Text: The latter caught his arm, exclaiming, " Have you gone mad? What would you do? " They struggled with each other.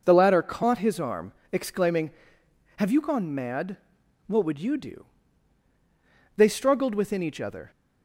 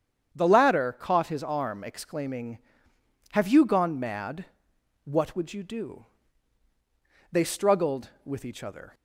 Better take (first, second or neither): second